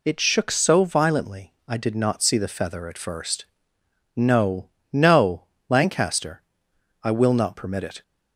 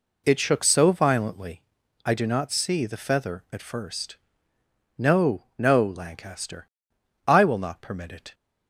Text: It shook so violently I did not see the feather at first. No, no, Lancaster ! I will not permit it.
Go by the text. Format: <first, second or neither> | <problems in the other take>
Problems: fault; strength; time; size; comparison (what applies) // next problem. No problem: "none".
first | pauses between "violently" and "I"; at 1.6 s; 0.44 s long; slight in the first // says "do" for "did"; at 2.1 s